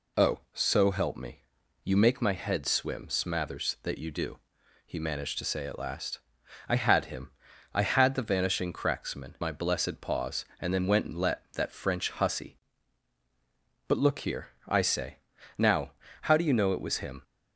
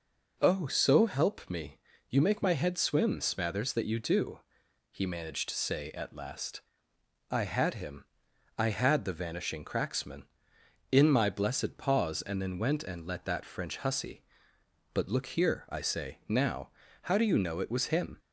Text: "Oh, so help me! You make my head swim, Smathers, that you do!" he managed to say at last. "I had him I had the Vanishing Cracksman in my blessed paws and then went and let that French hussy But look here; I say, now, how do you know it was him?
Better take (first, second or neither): second